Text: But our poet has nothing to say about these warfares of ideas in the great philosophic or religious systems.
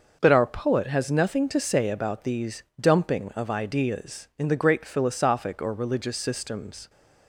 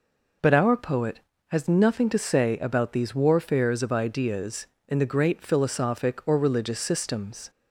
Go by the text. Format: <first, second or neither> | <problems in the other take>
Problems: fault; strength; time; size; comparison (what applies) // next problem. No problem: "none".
second | says "dumping" for "warfares"; at 2.7 s